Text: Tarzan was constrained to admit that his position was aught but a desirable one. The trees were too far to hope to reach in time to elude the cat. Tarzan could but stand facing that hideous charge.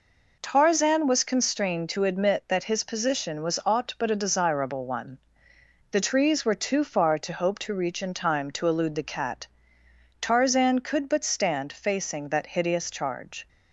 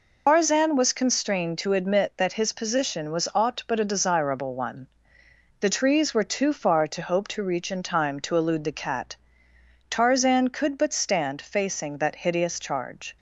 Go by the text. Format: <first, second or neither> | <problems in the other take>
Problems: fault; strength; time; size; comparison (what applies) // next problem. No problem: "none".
first | loses the start of "Tarzan"; at 0.2 s; 175 ms